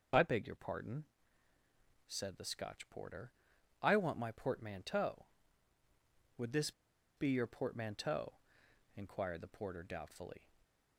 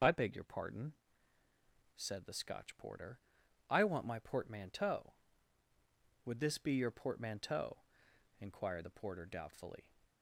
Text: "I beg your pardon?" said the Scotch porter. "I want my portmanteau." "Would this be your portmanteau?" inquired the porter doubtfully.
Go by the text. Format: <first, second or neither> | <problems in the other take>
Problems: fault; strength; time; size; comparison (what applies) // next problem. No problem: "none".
second | pauses between "this" and "be"; noticeable; at 6.7 s; 0.46 s long // stays silent after the last word; slight; from 10.3 s on; 0.6 s long